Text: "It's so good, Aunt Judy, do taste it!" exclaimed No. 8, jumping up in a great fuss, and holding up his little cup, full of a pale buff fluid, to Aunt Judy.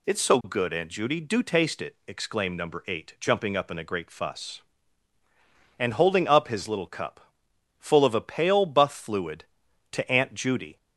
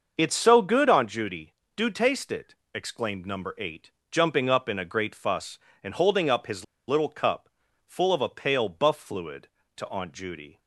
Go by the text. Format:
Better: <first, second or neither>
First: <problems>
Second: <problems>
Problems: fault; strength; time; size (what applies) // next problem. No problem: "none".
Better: first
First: none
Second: starts louder than the rest; until 1.1 s; 6 dB // pauses between "his" and "little"; slight; at 6.6 s; 0.23 s long